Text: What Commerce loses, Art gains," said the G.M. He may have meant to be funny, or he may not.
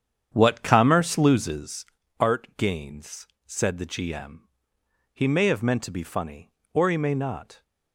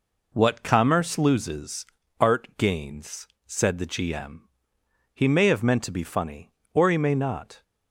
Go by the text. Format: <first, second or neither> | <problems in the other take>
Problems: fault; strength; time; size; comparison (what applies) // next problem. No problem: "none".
second | starts louder than the rest; strong; until 1.8 s; 8.5 dB